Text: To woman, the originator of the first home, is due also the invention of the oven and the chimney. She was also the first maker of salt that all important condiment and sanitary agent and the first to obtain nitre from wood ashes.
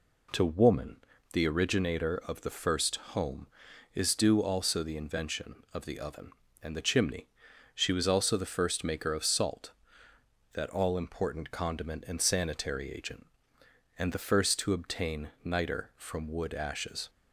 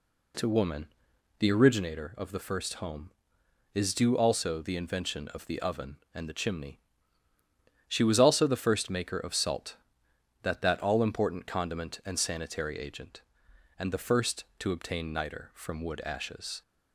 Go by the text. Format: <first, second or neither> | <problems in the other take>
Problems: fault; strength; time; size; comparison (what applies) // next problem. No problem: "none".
first | says "that" twice; at 10.5 s